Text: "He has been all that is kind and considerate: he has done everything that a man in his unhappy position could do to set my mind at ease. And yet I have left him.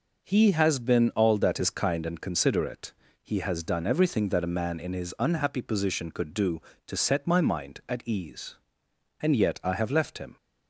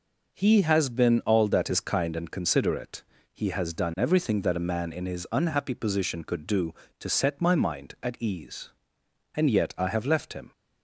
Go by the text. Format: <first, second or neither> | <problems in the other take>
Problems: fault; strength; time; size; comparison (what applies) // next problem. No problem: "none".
neither | none